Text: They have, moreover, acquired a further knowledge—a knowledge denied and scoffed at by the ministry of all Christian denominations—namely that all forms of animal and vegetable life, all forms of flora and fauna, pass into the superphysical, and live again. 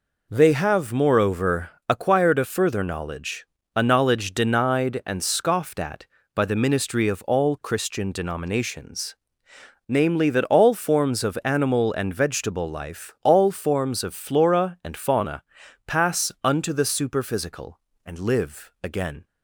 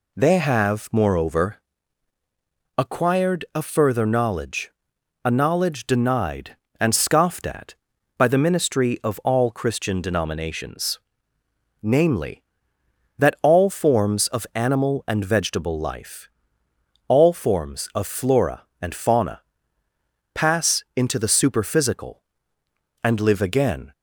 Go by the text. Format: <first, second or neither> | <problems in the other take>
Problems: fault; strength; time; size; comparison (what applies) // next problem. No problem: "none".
second | says "unto" for "into"; at 16.4 s